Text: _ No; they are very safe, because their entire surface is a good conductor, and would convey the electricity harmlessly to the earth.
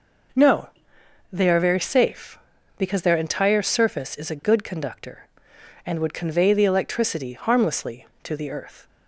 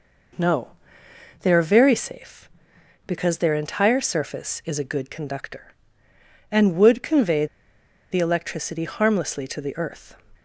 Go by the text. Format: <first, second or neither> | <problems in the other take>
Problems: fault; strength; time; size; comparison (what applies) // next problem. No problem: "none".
first | pauses between "convey" and "the"; noticeable; at 7.4 s; 0.65 s long